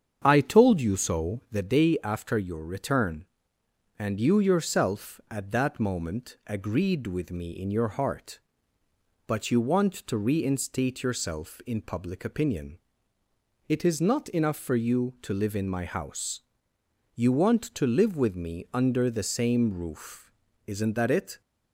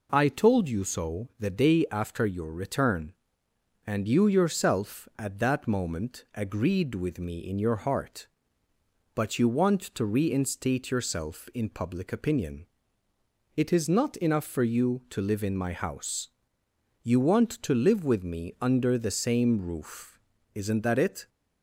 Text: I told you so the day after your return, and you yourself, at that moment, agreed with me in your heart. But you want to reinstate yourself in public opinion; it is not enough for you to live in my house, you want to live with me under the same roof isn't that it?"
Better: second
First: starts louder than the rest; strong; until 1.7 s; 8 dB // pauses between "roof" and "isn't"; slight; at 20.3 s; 0.36 s long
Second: pauses between "roof" and "isn't"; slight; at 20.1 s; 0.36 s long

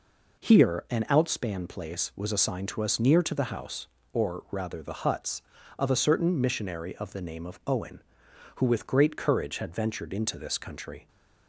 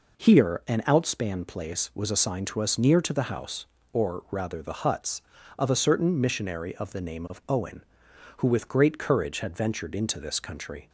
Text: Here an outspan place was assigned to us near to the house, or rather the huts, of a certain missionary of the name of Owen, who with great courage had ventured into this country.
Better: neither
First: none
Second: none

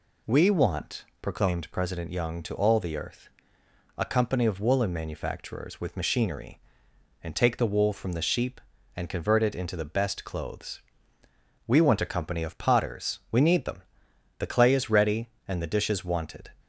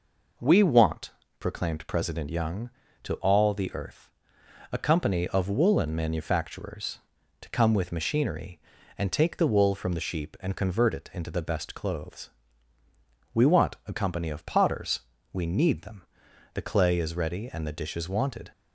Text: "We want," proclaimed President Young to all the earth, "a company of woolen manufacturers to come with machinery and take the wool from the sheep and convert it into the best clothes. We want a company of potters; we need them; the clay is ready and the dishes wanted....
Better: second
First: skips "to come"; at 5.8 s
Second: none

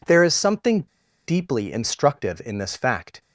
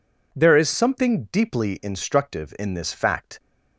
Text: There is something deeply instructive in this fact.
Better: second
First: pauses between "something" and "deeply"; at 0.8 s; 0.45 s long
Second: none

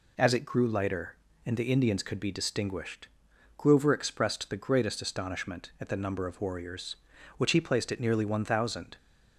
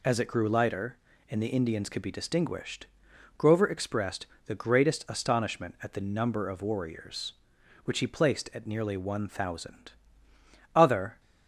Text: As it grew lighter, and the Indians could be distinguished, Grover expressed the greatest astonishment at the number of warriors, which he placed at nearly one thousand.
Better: first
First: none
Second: pauses between "expressed" and "the"; slight; at 4.2 s; 0.20 s long // goes on to say "Other"; slight; from 10.7 s on; 0.46 s long

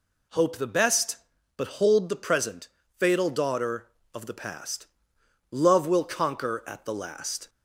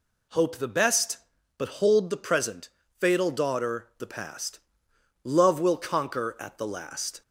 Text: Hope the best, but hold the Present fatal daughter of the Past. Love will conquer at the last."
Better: first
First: pauses between "Present" and "fatal"; slight; at 2.6 s; 0.32 s long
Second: pauses between "Present" and "fatal"; slight; at 2.6 s; 0.32 s long // skips "of"; at 3.9 s

